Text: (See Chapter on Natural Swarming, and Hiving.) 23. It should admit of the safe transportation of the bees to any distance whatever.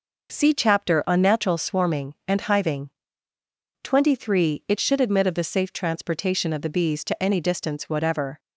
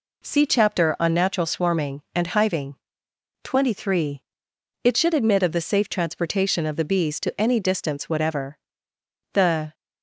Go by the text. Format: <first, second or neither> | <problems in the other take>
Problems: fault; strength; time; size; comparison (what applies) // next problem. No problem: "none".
first | goes on to say "The"; slight; from 9.3 s on; 0.40 s long